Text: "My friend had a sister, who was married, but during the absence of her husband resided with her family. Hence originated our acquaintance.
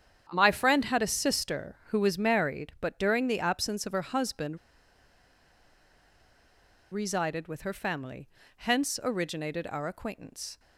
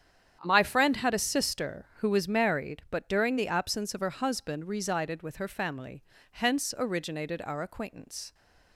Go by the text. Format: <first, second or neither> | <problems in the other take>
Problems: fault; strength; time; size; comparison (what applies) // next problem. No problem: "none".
second | starts louder than the rest; strong; until 1.3 s; 8.5 dB; strong in the second // pauses between "husband" and "resided"; strong; at 4.5 s; 2.3 s long